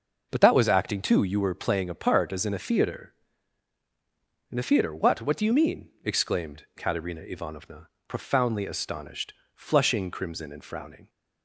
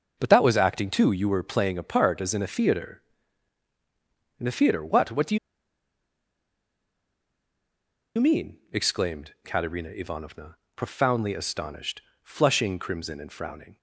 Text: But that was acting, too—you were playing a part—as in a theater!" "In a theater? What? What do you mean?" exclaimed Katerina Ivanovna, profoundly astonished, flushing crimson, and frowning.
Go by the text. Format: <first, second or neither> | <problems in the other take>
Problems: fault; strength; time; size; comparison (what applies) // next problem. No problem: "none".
first | pauses between "do" and "you"; strong; at 5.3 s; 2.8 s long